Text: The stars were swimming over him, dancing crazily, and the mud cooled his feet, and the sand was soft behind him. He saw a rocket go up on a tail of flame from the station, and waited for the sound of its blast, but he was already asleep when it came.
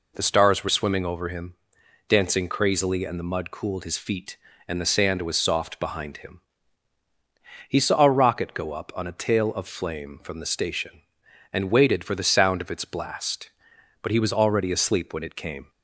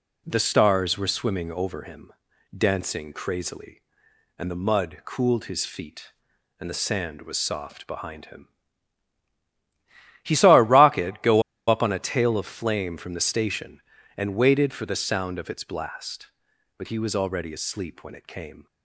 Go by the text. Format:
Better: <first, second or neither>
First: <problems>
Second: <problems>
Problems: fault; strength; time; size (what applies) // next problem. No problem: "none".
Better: first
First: none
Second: pauses between "go" and "up"; slight; at 11.4 s; 0.25 s long